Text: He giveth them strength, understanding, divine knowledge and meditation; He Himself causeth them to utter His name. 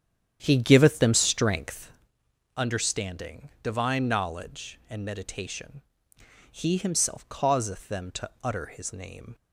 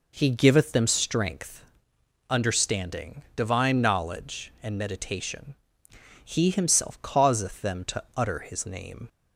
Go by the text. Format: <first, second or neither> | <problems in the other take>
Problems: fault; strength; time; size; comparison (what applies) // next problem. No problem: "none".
second | starts louder than the rest; strong; until 2.1 s; 9.5 dB // pauses between "to" and "utter"; slight; at 8.2 s; 0.16 s long; slight in the second